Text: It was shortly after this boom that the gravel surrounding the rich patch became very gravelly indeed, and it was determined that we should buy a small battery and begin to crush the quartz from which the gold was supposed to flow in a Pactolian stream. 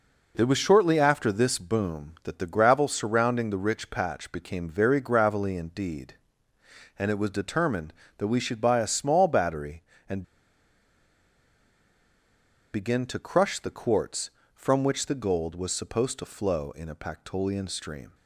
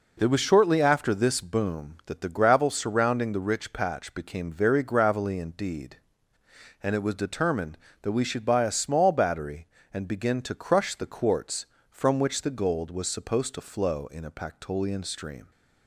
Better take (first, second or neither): second